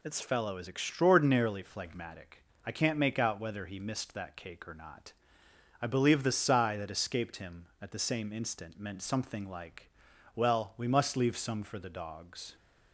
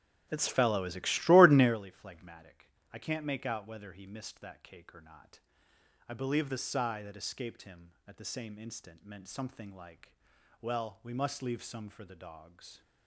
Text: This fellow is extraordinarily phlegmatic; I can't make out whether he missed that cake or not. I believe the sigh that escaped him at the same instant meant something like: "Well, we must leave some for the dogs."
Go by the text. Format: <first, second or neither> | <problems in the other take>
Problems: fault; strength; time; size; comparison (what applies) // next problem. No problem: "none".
first | starts louder than the rest; strong; until 1.8 s; 9 dB